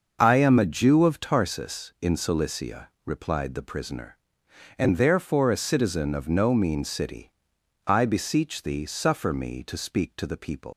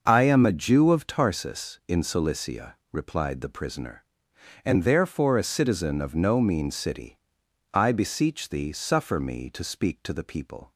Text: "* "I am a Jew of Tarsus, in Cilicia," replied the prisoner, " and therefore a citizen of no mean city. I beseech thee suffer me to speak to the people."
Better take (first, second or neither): second